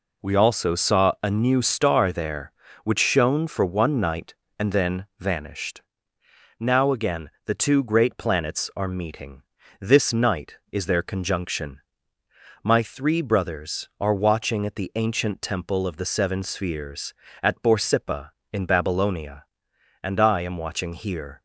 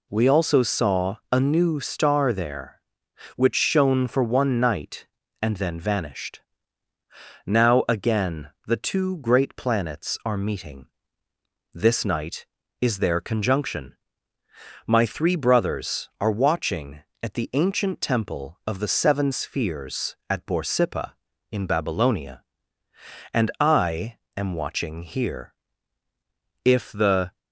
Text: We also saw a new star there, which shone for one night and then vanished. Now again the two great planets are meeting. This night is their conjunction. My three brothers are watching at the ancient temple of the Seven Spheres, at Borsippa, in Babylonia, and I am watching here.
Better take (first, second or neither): first